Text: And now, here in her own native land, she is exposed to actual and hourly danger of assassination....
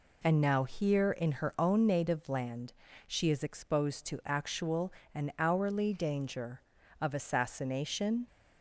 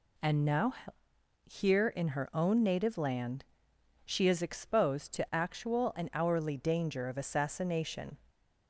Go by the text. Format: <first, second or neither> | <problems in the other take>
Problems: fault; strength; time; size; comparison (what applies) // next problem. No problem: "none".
neither | none